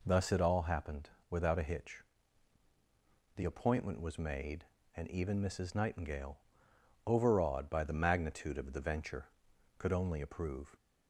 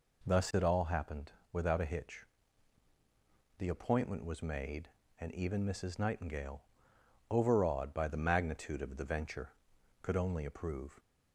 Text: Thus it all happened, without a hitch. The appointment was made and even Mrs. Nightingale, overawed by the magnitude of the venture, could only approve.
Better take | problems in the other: neither | none

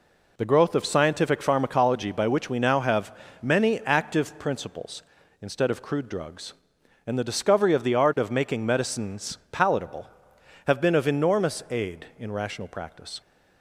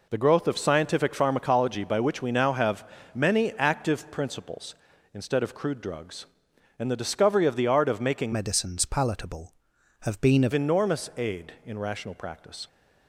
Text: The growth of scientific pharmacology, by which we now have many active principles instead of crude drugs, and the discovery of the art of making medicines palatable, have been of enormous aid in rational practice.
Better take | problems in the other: first | pauses between "have" and "many"; slight; at 2.8 s; 0.28 s long; slight in the first // changes voice from "medicines" to "of"; from 8.3 to 10.5 s; 2.2 s long

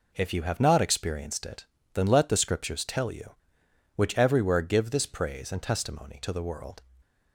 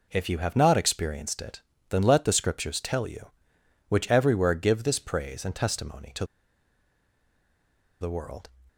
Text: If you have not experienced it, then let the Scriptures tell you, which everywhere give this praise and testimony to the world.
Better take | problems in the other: first | pauses between "to" and "the"; strong; at 6.2 s; 1.7 s long

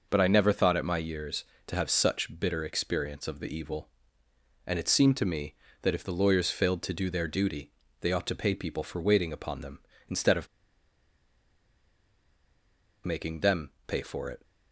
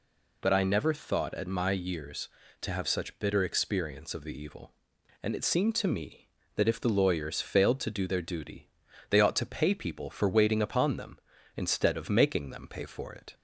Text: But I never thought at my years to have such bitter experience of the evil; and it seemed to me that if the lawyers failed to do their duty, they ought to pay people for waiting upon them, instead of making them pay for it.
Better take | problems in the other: second | pauses between "of" and "making"; strong; at 10.4 s; 2.5 s long // pauses between "them" and "pay"; slight; at 13.7 s; 0.16 s long

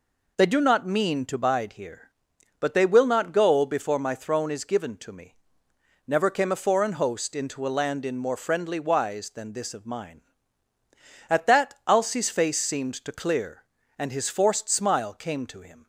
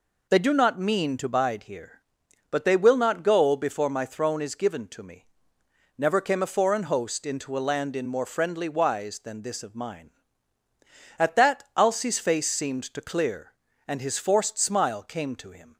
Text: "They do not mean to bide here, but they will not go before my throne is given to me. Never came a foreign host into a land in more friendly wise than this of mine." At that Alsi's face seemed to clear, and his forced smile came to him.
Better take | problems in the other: neither | none

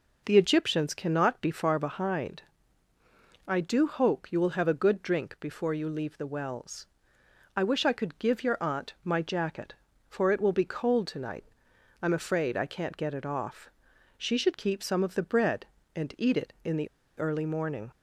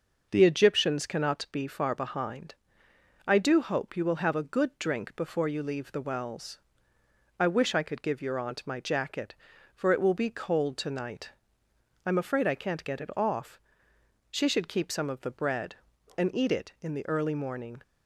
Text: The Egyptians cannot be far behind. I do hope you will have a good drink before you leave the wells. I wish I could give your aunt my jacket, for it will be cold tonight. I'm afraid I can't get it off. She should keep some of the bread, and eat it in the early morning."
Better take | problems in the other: second | pauses between "the" and "early"; slight; at 16.8 s; 0.29 s long

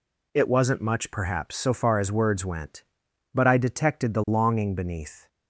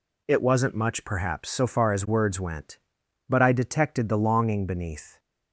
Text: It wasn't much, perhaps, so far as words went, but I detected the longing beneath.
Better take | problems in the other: neither | none

